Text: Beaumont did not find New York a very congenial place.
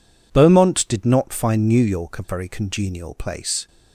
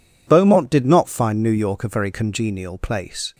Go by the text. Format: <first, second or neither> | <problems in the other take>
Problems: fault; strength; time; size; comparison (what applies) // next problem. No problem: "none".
neither | none